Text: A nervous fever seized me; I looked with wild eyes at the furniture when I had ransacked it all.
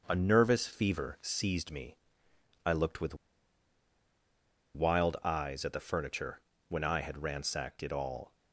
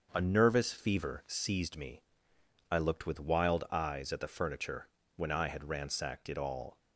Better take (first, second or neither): second